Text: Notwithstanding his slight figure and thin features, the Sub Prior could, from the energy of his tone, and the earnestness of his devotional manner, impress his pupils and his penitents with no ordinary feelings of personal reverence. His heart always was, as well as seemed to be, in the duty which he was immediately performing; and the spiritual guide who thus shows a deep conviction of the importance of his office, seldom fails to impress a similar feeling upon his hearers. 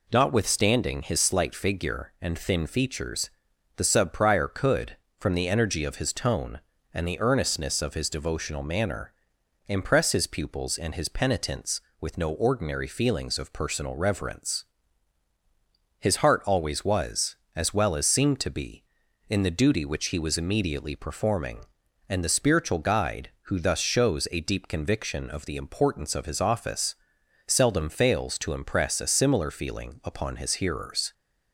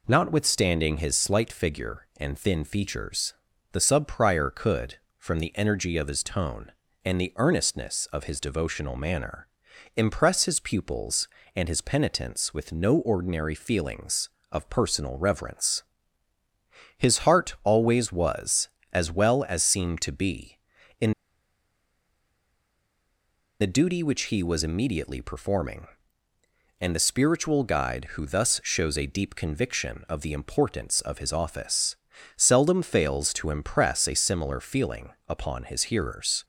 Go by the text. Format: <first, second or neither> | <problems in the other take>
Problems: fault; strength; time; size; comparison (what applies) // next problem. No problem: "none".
first | pauses between "in" and "the"; strong; at 21.1 s; 2.4 s long // pauses between "feeling" and "upon"; slight; at 35.1 s; 0.18 s long